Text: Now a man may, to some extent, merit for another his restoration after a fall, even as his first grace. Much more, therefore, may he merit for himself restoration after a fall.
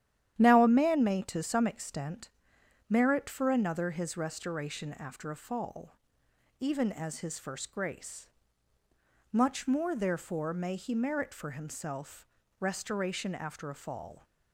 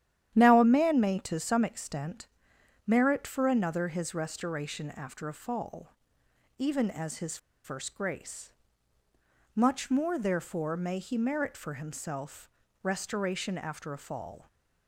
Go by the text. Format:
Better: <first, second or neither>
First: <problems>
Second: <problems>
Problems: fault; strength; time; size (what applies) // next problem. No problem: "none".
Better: first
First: starts louder than the rest; strong; until 1.4 s; 11 dB // pauses between "himself" and "restoration"; slight; at 12.2 s; 0.32 s long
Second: starts louder than the rest; strong; until 1.4 s; 11 dB // pauses between "his" and "first"; slight; at 7.3 s; 0.27 s long // pauses between "himself" and "restoration"; slight; at 12.4 s; 0.32 s long